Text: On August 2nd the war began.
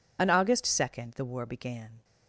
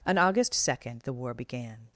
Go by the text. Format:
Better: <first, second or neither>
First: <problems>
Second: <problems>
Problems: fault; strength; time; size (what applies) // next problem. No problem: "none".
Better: second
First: loses the start of "On"; at 0.1 s; 60 ms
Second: none